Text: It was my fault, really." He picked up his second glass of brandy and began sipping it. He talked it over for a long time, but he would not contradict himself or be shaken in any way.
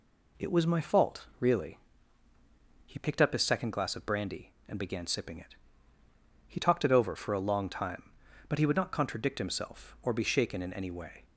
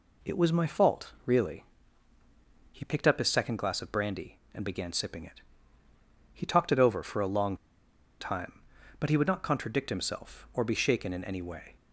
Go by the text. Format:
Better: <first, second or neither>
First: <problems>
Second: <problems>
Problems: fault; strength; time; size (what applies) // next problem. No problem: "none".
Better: first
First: none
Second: pauses between "long" and "time"; noticeable; at 7.5 s; 0.62 s long